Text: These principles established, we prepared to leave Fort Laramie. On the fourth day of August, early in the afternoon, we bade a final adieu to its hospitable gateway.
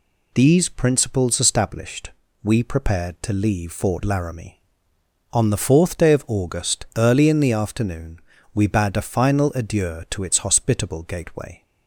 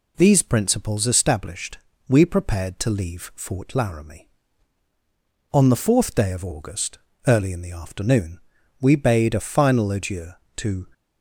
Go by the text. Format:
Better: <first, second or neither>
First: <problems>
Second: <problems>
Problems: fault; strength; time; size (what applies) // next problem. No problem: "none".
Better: first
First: none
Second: stops before "its hospitable gateway"; at 10.9 s